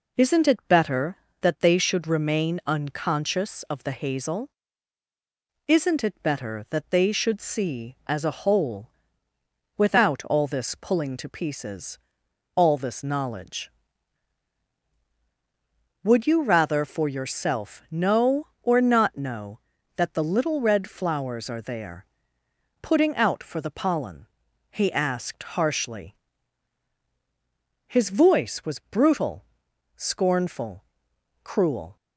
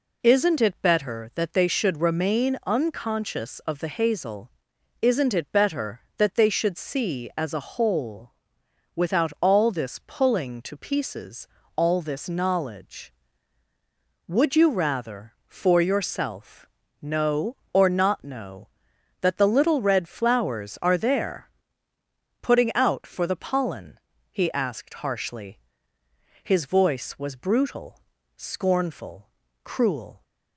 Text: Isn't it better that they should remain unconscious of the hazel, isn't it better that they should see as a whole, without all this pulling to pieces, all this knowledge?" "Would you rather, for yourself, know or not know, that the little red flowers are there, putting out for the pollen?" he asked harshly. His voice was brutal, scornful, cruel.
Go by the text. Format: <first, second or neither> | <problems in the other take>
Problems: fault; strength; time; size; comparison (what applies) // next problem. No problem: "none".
neither | none